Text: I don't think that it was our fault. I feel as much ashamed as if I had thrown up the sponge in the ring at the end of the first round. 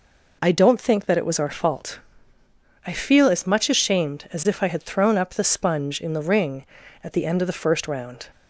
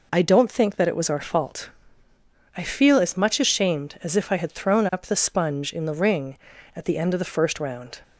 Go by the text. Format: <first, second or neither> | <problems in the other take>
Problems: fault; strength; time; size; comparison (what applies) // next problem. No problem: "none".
neither | none